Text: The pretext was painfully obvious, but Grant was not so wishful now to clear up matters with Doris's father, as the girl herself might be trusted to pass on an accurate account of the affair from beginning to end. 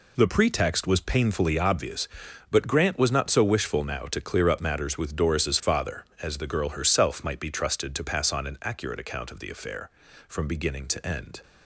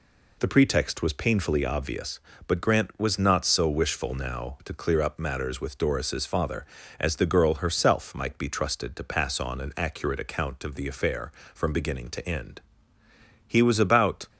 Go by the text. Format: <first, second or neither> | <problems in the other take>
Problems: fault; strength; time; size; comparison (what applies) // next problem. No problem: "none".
first | goes on to say "He was about"; noticeable; from 13.4 s on; 0.82 s long